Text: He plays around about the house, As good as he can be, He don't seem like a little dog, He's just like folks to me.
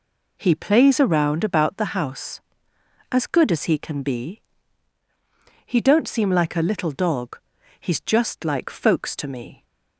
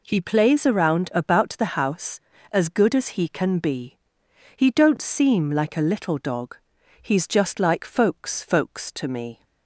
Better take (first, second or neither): first